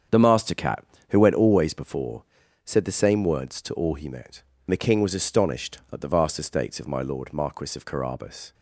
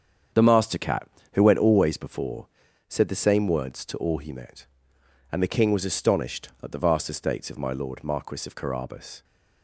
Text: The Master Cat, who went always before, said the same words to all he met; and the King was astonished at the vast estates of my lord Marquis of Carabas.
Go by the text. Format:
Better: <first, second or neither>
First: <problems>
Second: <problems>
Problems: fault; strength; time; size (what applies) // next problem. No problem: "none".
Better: second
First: starts louder than the rest; strong; until 1.3 s; 7.5 dB // skips "and"; at 4.5 s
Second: starts louder than the rest; strong; until 1.5 s; 7.5 dB